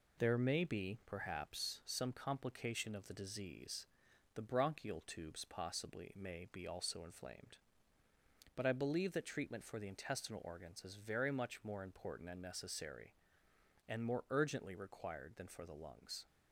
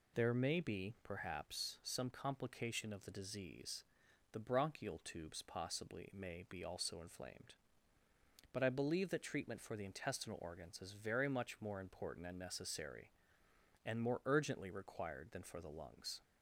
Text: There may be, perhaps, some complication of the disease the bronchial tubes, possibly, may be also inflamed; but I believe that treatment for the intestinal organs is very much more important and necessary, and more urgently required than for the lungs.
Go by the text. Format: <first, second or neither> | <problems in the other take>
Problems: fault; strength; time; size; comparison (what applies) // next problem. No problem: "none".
second | gets quieter; noticeable; throughout; 4.5 dB // pauses between "disease" and "the"; noticeable; at 3.8 s; 0.48 s long; noticeable in the second